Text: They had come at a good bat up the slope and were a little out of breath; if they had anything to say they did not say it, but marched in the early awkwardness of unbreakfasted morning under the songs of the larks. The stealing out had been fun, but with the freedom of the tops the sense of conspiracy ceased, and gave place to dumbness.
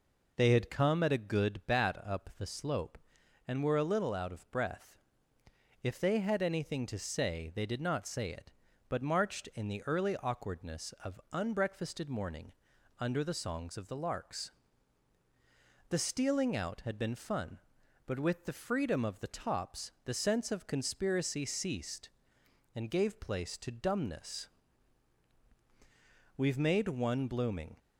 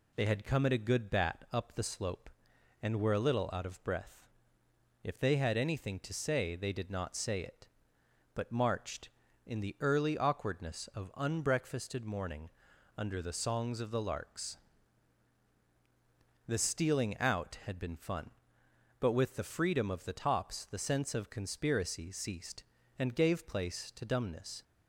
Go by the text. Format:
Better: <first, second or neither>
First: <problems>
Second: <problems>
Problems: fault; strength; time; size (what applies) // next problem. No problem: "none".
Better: second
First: pauses between "morning" and "under"; noticeable; at 12.5 s; 0.46 s long // goes on to say "We've made one blooming"; from 26.3 s on; 1.4 s long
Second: pauses between "morning" and "under"; at 12.5 s; 0.44 s long